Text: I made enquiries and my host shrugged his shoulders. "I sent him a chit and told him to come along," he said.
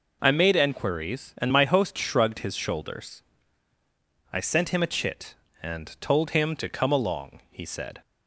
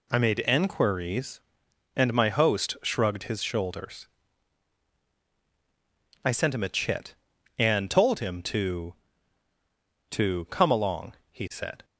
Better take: first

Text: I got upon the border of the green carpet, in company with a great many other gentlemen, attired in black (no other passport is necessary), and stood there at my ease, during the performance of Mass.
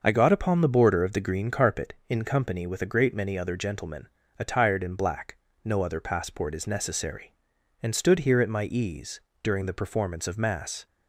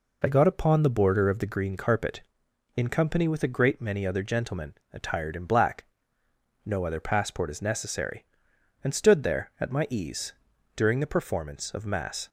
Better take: second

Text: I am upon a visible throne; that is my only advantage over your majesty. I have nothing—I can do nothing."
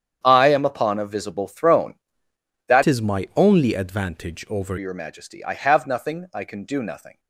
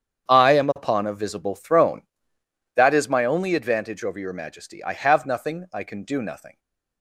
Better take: second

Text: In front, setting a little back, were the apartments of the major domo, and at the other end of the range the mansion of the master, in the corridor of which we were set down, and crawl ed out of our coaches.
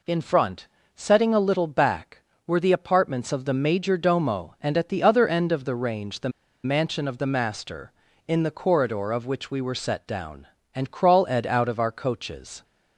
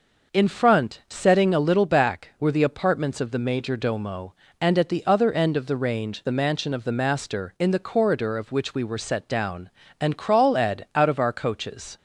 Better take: second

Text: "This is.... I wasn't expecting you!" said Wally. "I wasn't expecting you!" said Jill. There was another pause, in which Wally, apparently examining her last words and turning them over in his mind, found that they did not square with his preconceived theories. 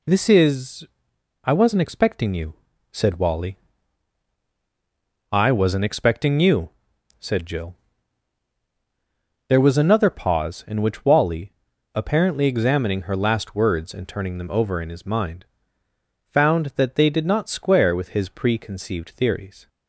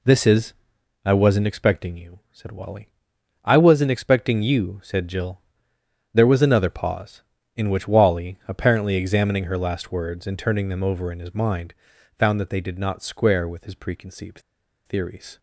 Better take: first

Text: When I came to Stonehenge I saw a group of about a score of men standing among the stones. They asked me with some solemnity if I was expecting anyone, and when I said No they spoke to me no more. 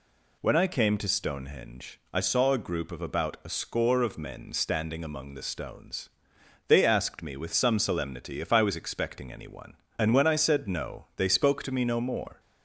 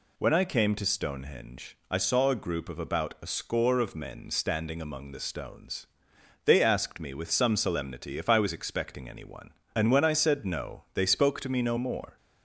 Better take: neither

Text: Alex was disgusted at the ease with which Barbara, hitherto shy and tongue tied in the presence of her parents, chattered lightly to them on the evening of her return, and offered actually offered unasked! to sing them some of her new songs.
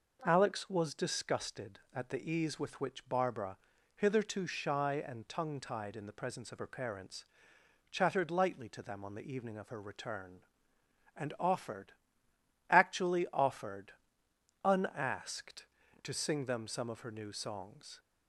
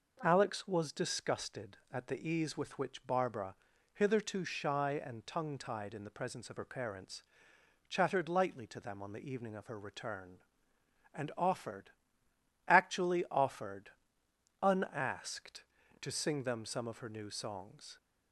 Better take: neither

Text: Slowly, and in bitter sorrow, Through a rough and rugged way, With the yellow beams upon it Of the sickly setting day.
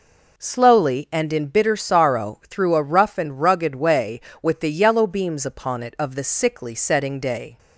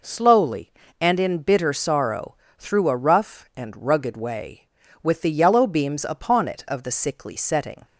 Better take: first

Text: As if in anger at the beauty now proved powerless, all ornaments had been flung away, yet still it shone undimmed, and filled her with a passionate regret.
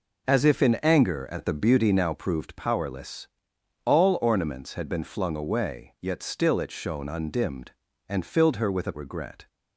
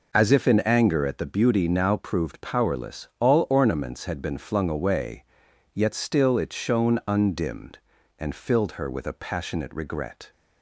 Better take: second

